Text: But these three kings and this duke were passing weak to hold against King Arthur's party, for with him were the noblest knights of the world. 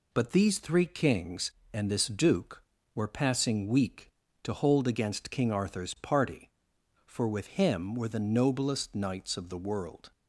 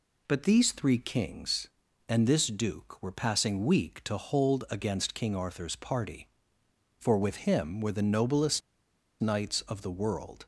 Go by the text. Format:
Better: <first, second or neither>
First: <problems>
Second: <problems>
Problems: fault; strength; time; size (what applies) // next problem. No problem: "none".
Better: first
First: none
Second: pauses between "noblest" and "knights"; noticeable; at 8.6 s; 0.61 s long